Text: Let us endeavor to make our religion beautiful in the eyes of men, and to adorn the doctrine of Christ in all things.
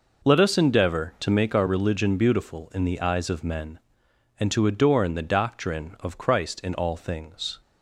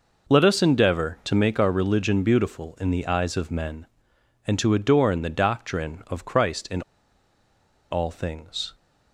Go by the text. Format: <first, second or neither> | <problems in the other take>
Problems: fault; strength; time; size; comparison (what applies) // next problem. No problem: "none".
first | pauses between "in" and "all"; at 6.8 s; 1.0 s long